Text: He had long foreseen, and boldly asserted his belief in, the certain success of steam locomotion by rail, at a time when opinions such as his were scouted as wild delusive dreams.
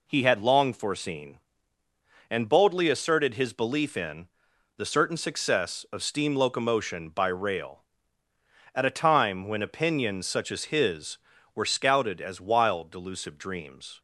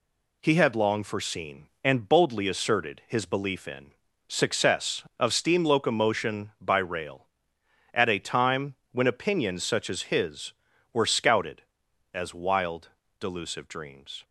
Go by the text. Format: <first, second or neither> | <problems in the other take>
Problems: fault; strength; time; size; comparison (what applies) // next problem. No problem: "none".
first | skips "the certain"; at 4.0 s // pauses between "time" and "when"; slight; at 8.7 s; 0.18 s long // pauses between "wild" and "delusive"; slight; at 12.8 s; 0.32 s long